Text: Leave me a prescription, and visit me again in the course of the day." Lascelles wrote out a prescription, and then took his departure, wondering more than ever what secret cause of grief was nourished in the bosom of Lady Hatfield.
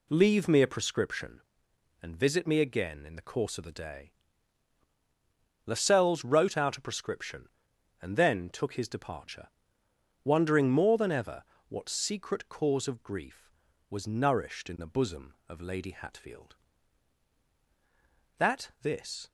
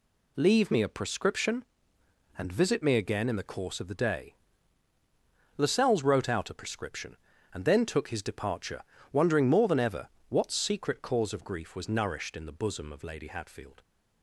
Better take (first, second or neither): second